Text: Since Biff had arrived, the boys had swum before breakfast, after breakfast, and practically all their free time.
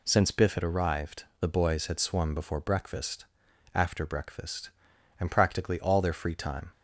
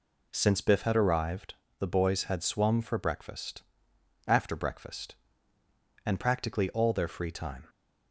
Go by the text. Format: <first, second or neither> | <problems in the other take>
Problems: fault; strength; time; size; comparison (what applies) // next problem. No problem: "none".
first | says "for" for "before"; at 2.8 s